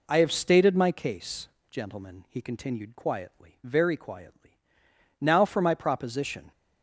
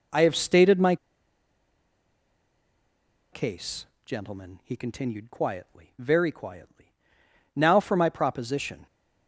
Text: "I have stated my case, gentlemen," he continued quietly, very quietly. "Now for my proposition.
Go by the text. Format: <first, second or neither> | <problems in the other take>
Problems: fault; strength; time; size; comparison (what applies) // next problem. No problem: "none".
first | pauses between "my" and "case"; strong; at 0.9 s; 2.3 s long